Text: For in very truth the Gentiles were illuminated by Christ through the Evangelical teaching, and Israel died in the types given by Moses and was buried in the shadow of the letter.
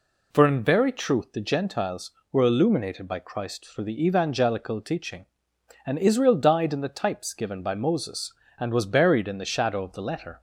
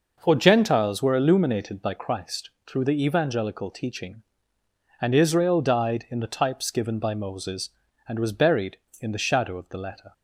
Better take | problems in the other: first | skips "in very truth the"; at 0.3 s // pauses between "Christ" and "through"; slight; at 2.4 s; 0.18 s long

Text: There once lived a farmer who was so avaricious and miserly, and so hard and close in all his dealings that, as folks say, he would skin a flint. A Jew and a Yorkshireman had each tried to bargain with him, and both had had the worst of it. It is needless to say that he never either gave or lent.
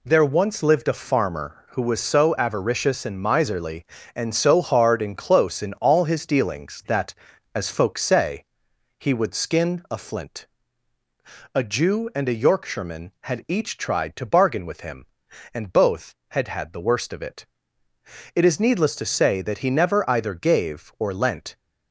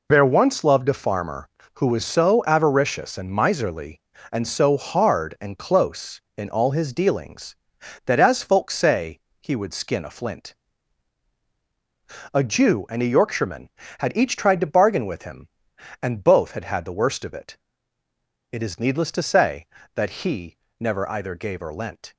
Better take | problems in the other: first | says "loved" for "lived"; at 0.6 s // pauses between "he" and "never"; slight; at 20.5 s; 0.24 s long

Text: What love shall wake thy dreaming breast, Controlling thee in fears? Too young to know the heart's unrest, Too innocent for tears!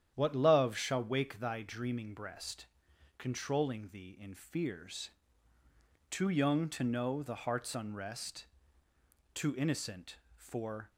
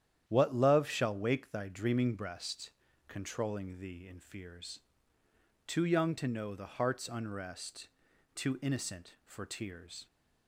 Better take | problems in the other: second | starts louder than the rest; strong; until 1.1 s; 9.5 dB; strong in the second // stops before "tears"; at 10.8 s

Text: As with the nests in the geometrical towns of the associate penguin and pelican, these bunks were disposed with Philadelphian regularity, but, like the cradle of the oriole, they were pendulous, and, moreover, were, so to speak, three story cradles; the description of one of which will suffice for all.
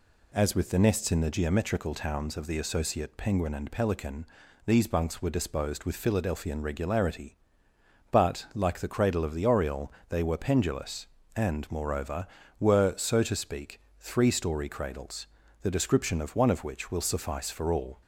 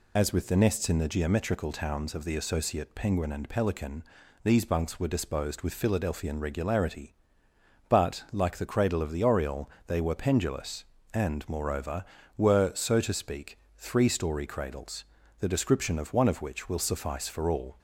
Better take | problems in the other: first | loses the start of "As"; at 0.1 s; 40 ms

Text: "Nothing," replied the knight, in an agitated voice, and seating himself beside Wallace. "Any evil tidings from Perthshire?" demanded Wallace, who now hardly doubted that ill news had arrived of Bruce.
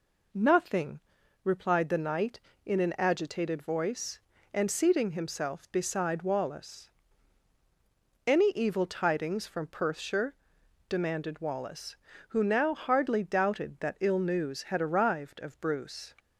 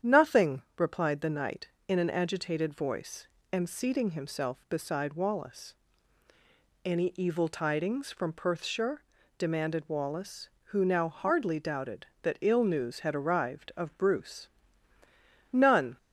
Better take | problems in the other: first | starts louder than the rest; strong; until 1.2 s; 9 dB // goes on to say "None"; slight; from 15.5 s on; 0.46 s long

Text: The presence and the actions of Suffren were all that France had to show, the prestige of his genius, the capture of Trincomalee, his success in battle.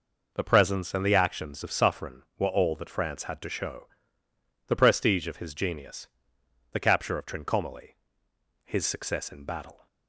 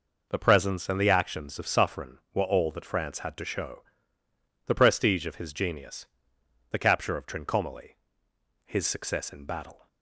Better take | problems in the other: neither | none

